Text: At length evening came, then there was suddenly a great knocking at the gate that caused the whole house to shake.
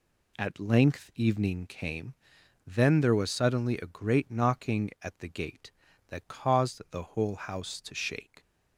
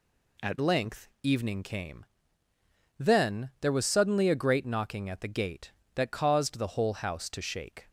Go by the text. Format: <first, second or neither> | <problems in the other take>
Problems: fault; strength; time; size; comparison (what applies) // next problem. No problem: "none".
first | changes voice at "length"; from 0.5 s on; 7.3 s long